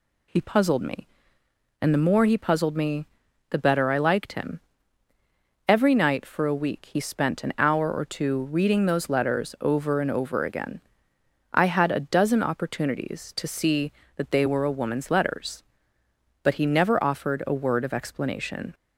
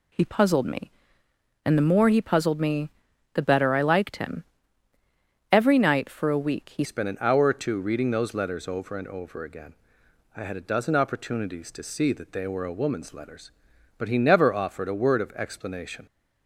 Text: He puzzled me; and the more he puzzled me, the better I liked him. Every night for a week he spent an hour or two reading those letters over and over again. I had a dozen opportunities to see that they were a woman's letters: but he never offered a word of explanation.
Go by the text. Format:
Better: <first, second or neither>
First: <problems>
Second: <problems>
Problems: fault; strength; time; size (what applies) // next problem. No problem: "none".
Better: first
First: none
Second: changes voice at "spent"; from 6.8 s on; 9.2 s long